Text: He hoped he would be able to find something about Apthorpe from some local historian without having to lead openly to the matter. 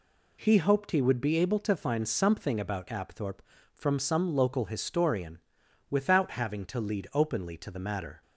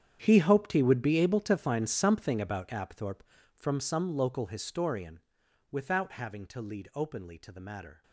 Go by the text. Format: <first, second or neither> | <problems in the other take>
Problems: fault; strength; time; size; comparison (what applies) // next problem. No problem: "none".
first | gets quieter; strong; throughout; 16.5 dB // pauses between "historian" and "without"; noticeable; at 5.2 s; 0.50 s long; noticeable in the first